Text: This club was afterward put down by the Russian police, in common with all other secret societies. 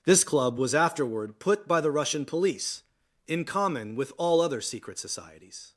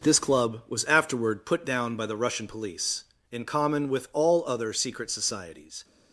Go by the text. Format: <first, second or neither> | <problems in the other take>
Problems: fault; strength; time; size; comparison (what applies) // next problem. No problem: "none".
second | skips "down"; at 1.6 s